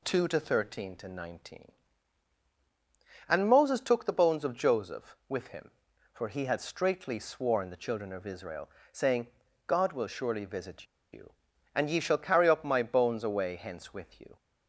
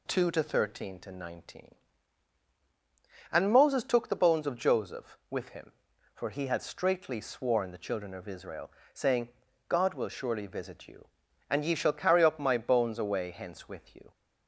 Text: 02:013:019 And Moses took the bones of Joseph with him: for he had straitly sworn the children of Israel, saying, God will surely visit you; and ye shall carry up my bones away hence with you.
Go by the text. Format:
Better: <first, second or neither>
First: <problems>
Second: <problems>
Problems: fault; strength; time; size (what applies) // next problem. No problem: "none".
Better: second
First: pauses between "visit" and "you"; slight; at 10.8 s; 0.27 s long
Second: none